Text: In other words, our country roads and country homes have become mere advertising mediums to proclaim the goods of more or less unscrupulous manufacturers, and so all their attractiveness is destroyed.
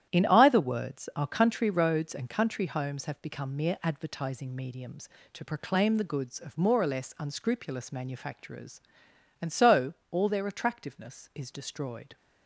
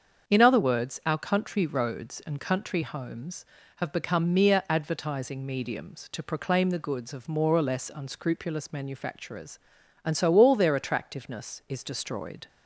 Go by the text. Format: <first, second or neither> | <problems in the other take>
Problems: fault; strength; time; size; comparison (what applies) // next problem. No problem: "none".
second | starts louder than the rest; strong; until 1.1 s; 11 dB; also in the second // says "either" for "other"; at 0.2 s // pauses between "so" and "all"; slight; at 9.9 s; 0.16 s long